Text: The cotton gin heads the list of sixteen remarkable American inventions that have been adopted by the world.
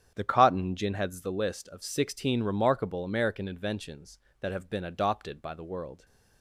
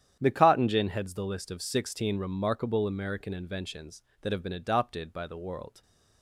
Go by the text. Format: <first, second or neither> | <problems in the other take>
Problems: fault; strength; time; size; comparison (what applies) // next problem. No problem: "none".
neither | starts louder than the rest; strong; the same in both